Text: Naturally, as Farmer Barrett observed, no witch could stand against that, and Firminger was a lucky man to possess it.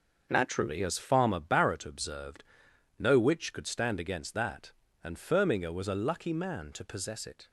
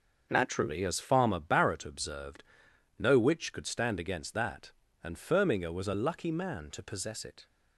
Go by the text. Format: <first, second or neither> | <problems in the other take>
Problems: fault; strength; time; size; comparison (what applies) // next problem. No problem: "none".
neither | starts louder than the rest; the same in both